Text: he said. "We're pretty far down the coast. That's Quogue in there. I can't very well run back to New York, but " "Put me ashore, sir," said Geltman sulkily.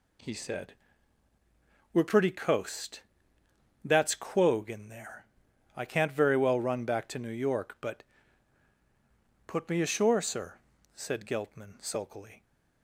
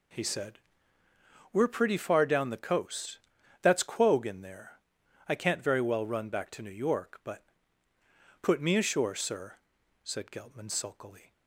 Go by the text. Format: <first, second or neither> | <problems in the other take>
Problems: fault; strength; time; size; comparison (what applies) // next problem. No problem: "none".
second | skips "far down the"; at 2.3 s